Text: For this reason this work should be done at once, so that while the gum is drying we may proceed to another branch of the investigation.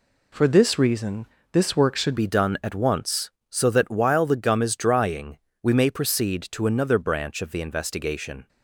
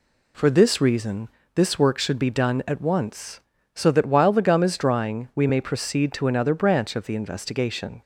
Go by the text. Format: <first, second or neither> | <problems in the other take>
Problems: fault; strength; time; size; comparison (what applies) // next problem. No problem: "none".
second | pauses between "reason" and "this"; slight; at 1.2 s; 0.24 s long; slight in the second // changes voice at "be"; from 2.1 s on; 6.3 s long // pauses between "drying" and "we"; slight; at 5.3 s; 0.24 s long